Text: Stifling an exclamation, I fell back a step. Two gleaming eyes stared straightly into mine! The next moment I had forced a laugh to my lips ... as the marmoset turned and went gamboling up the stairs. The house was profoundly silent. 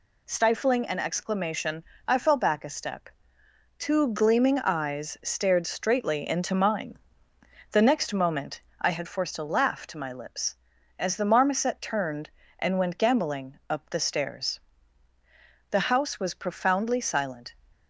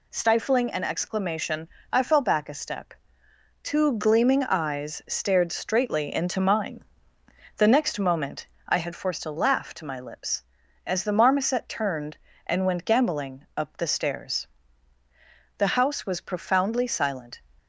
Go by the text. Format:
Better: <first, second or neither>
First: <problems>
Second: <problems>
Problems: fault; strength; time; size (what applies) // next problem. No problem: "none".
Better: neither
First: pauses between "moment" and "I"; slight; at 8.6 s; 0.20 s long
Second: pauses between "moment" and "I"; slight; at 8.4 s; 0.22 s long